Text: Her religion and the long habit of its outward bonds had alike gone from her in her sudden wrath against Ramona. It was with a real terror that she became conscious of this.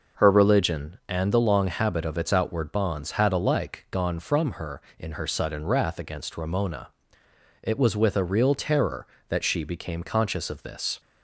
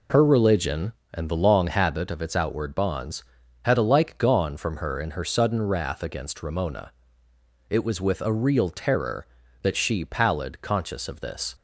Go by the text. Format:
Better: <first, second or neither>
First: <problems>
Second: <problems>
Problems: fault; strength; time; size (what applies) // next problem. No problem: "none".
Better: first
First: none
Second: says "pallid" for "became"; at 10.0 s